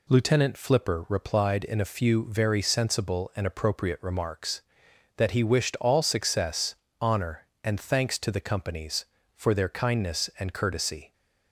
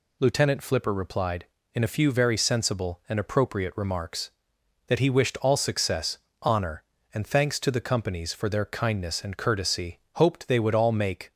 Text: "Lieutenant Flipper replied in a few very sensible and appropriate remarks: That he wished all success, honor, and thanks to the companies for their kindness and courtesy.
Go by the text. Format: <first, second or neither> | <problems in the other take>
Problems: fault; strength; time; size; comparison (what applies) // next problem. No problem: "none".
first | goes on to say "Hoped they would all make"; noticeable; from 10.1 s on; 1.2 s long